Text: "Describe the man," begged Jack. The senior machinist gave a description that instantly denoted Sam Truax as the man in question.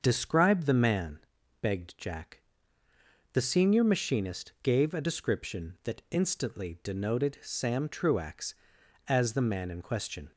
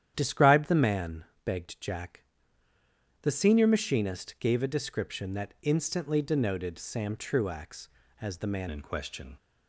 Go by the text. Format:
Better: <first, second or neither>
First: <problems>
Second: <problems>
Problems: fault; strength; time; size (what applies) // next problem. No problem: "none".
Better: first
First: starts louder than the rest; until 1.0 s; 6.5 dB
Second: starts louder than the rest; strong; until 1.1 s; 10 dB // changes voice at "in"; from 8.7 s on; 0.6 s long